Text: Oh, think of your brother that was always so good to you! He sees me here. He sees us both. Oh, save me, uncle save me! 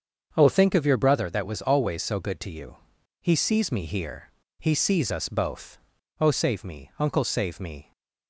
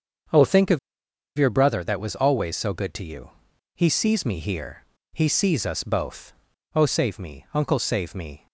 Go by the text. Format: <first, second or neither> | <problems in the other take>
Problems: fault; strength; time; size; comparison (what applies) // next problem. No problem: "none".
first | starts louder than the rest; until 1.9 s; 7 dB; also in the first // pauses between "of" and "your"; noticeable; at 0.7 s; 0.59 s long